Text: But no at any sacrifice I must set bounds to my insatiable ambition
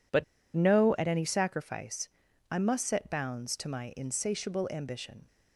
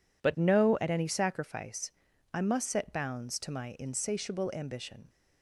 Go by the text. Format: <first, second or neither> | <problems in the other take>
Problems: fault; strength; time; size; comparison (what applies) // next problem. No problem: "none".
second | pauses between "But" and "no"; slight; at 0.2 s; 0.30 s long // pauses between "sacrifice" and "I"; at 2.0 s; 0.44 s long; also in the second